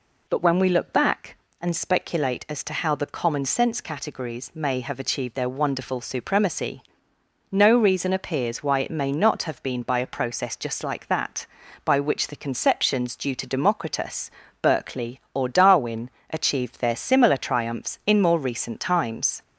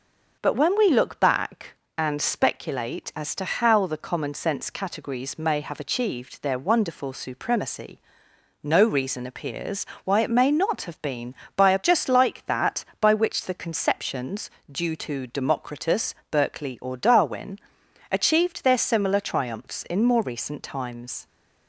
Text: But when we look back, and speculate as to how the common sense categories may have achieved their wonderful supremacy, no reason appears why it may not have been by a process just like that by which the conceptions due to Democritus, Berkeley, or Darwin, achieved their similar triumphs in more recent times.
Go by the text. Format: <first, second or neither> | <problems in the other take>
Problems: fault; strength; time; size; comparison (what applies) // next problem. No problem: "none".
first | pauses between "appears" and "why"; slight; at 9.8 s; 0.20 s long // skips "process"; at 11.8 s // pauses between "conceptions" and "due"; slight; at 14.5 s; 0.20 s long